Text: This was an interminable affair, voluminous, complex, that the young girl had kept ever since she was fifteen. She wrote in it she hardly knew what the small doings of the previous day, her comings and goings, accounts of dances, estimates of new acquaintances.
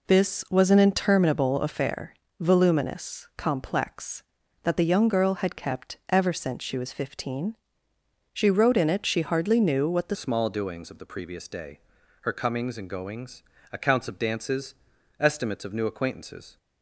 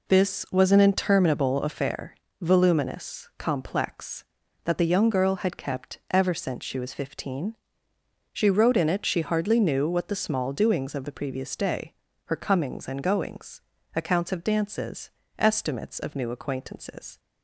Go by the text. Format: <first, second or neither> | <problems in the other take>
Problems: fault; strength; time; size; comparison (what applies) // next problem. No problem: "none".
second | changes voice at "small"; from 10.1 s on; 6.4 s long